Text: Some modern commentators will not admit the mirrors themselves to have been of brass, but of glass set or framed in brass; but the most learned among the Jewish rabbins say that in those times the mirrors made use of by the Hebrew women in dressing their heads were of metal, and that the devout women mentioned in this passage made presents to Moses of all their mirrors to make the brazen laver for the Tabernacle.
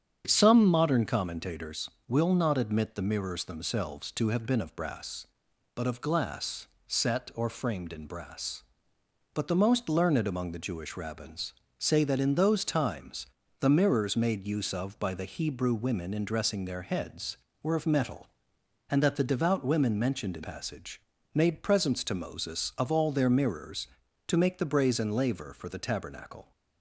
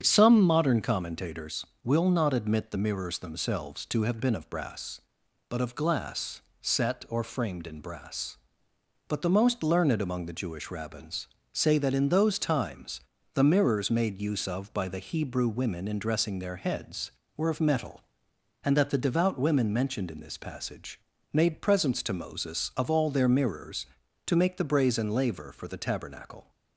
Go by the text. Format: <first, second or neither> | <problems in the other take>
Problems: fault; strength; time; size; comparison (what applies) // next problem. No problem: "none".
second | starts louder than the rest; strong; until 1.2 s; 8.5 dB; strong in the second // pauses between "glass" and "set"; slight; at 6.6 s; 0.22 s long; slight in the second // pauses between "rabbins" and "say"; slight; at 11.5 s; 0.26 s long; slight in the second // pauses between "times" and "the"; slight; at 13.2 s; 0.32 s long; slight in the second // skips "this"; at 20.4 s // pauses between "passage" and "made"; slight; at 20.9 s; 0.36 s long; slight in the second